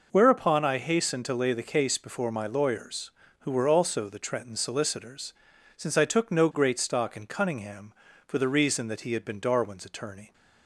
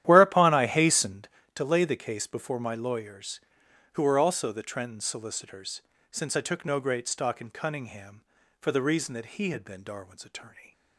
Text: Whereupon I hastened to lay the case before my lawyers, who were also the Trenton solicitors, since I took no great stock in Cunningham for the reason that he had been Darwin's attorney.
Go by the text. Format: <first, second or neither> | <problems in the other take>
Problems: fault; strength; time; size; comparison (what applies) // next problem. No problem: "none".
first | starts louder than the rest; strong; until 1.5 s; 12 dB